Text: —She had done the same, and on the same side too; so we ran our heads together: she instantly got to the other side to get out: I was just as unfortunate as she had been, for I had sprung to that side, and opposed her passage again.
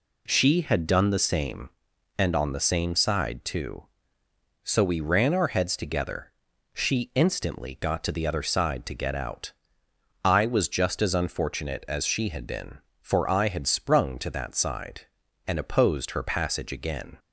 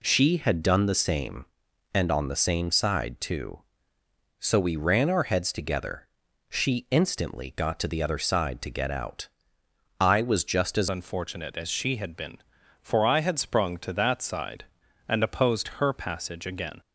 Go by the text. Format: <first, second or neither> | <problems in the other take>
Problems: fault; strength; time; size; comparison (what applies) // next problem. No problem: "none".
first | changes voice at "unfortunate"; from 10.8 s on; 6.0 s long